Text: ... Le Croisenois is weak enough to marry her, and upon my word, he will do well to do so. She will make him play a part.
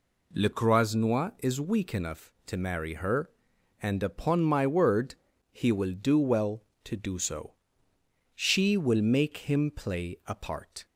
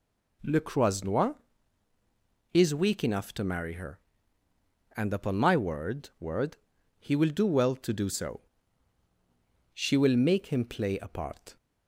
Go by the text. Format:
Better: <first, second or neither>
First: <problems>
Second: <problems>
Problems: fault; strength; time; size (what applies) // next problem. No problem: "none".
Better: first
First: none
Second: says "word" twice; at 6.1 s